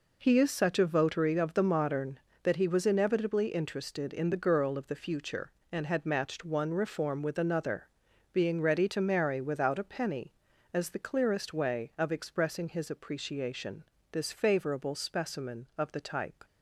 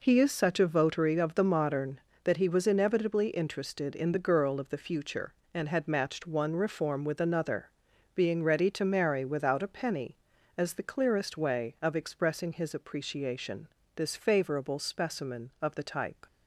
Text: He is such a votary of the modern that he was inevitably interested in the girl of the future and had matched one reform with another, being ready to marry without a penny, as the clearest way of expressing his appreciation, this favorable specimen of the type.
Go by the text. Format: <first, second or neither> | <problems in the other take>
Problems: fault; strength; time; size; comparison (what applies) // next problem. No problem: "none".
neither | none